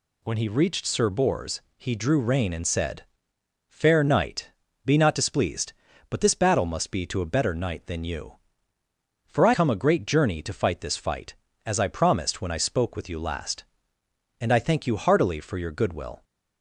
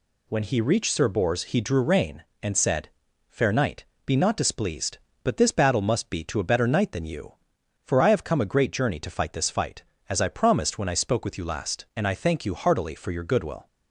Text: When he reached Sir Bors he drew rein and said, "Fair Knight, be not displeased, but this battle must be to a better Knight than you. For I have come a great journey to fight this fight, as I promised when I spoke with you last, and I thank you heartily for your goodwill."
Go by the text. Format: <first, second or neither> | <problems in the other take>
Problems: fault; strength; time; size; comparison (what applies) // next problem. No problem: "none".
second | pauses between "Bors" and "he"; slight; at 1.5 s; 0.16 s long // skips "have"; at 9.5 s